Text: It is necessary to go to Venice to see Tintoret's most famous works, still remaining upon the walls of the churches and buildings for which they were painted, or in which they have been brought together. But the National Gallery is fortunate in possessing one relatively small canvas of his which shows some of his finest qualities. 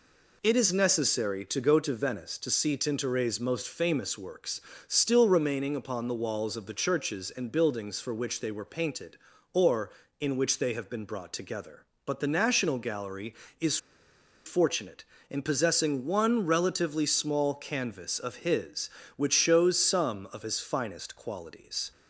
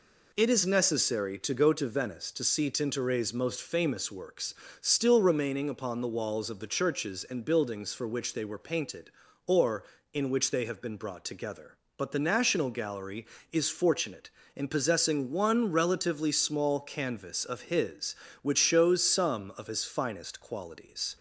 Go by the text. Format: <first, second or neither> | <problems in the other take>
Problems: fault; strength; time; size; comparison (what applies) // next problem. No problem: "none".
second | pauses between "is" and "fortunate"; noticeable; at 13.7 s; 0.69 s long